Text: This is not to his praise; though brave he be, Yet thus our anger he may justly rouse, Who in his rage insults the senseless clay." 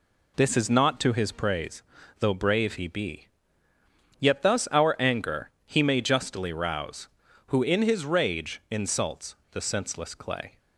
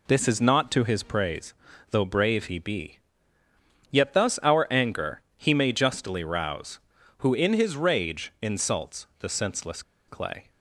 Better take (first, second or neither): first